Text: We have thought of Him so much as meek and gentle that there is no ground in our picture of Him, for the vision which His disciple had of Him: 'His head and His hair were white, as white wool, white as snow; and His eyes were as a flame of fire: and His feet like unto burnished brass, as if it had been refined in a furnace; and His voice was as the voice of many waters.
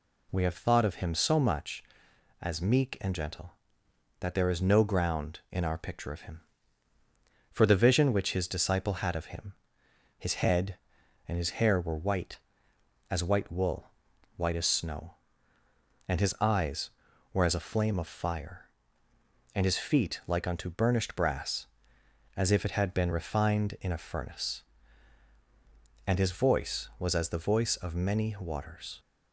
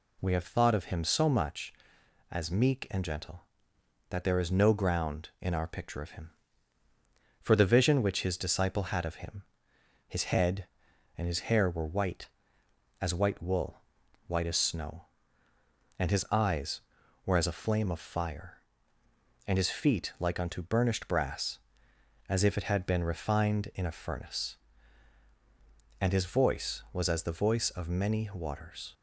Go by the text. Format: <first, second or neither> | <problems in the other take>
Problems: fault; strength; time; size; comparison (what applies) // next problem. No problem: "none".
neither | none